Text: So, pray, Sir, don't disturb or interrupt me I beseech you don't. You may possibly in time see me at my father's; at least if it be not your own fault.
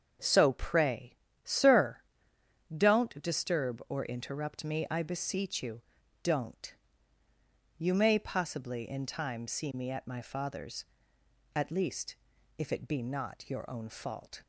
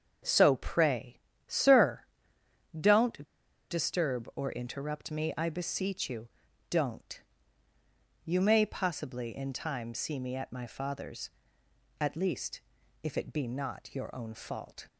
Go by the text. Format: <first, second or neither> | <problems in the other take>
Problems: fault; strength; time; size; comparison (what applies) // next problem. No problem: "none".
first | starts louder than the rest; until 1.5 s; 7 dB; also in the first // pauses between "don't" and "disturb"; at 3.2 s; 0.43 s long // pauses between "you" and "don't"; at 6.2 s; 0.42 s long; also in the first // pauses between "least" and "if"; at 12.5 s; 0.42 s long; also in the first